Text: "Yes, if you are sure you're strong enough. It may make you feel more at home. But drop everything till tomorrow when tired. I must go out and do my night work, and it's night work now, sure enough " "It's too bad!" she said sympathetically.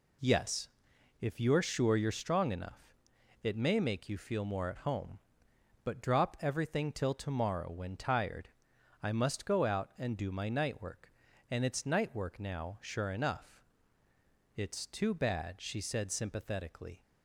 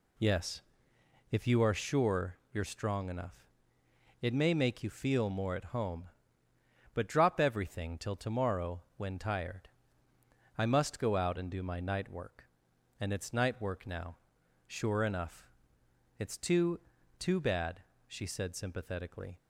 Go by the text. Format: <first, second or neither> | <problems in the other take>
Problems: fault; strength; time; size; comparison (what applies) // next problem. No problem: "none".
first | pauses between "tomorrow" and "when"; slight; at 8.8 s; 0.16 s long // says "too" twice; at 17.1 s